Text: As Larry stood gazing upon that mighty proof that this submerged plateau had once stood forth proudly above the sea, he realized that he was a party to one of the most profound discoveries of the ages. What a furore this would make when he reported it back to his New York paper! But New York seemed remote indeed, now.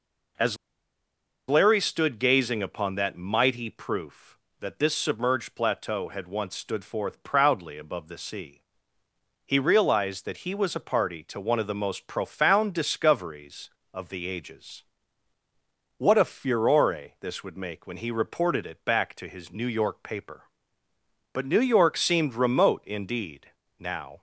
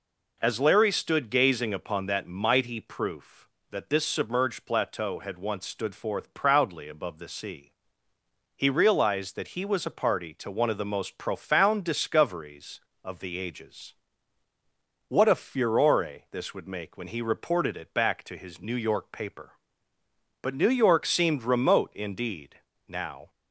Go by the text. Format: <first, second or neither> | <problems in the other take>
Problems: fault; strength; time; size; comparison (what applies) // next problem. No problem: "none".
second | pauses between "As" and "Larry"; noticeable; at 0.5 s; 0.92 s long